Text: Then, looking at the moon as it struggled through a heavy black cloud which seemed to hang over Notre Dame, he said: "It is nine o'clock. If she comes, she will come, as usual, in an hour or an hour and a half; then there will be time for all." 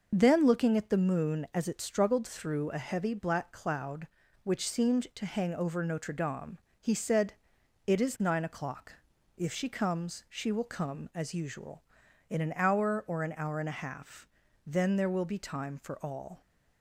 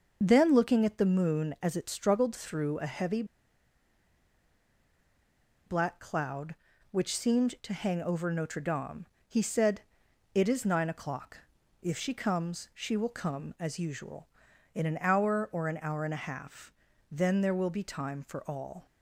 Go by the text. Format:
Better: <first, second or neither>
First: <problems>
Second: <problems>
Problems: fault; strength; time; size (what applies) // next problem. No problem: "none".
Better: first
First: none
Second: pauses between "heavy" and "black"; strong; at 3.2 s; 2.4 s long